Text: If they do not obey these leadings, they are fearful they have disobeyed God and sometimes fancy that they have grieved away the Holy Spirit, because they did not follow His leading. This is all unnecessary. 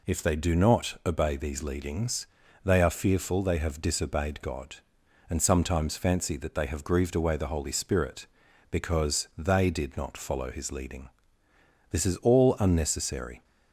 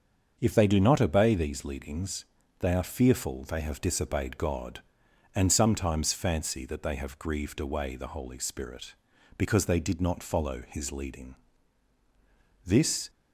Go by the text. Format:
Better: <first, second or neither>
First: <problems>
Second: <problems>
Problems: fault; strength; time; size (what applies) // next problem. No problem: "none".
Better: first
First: none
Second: starts louder than the rest; until 1.4 s; 7 dB // stops before "is all unnecessary"; at 13.0 s